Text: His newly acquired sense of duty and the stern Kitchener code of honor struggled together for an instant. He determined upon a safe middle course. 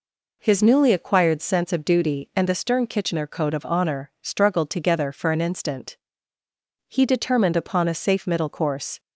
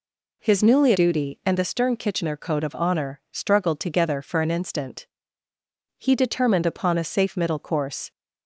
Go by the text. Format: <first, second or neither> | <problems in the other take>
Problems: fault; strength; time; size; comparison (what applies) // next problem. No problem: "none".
first | skips "acquired sense of"; at 0.9 s